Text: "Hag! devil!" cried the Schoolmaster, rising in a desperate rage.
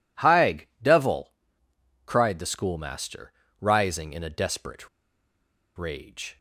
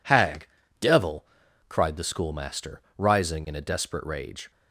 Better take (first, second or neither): second